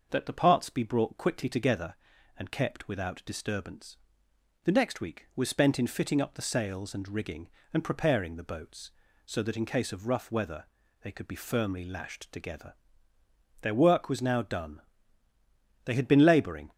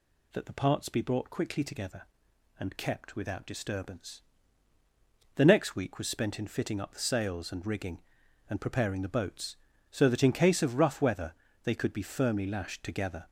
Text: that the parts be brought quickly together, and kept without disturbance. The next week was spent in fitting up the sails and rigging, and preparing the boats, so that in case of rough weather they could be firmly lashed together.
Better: second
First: pauses between "weather" and "they"; at 10.6 s; 0.38 s long // goes on to say "Their work was now done They had been labouring"; strong; from 13.6 s on; 3.1 s long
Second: pauses between "weather" and "they"; slight; at 11.3 s; 0.30 s long

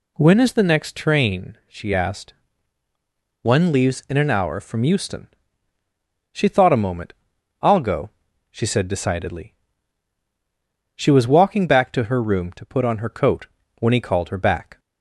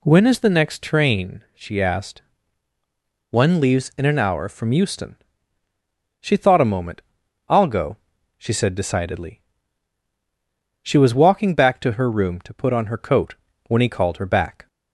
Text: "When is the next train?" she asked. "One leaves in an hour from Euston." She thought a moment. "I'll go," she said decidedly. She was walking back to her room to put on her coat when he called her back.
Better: neither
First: pauses between "coat" and "when"; slight; at 13.4 s; 0.30 s long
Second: pauses between "coat" and "when"; slight; at 13.3 s; 0.30 s long

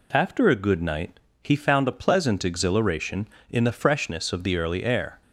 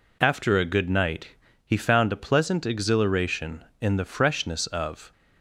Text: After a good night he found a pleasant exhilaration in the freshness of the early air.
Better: first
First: pauses between "night" and "he"; slight; at 1.2 s; 0.20 s long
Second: pauses between "night" and "he"; slight; at 1.3 s; 0.30 s long // stops before "the early air"; at 5.1 s

